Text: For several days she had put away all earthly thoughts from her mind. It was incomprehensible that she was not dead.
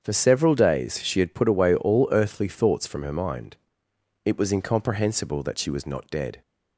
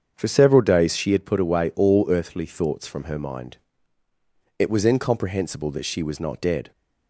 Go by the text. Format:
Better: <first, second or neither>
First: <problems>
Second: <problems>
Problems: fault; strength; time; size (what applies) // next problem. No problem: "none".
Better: neither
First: starts louder than the rest; strong; until 1.0 s; 7.5 dB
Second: starts louder than the rest; strong; until 1.1 s; 7.5 dB